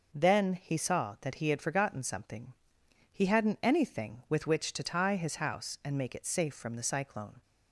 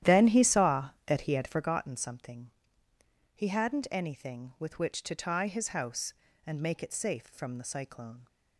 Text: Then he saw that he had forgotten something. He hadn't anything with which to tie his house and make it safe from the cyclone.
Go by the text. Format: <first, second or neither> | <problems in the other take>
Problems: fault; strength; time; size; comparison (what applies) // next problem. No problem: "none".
first | starts louder than the rest; strong; until 1.7 s; 11.5 dB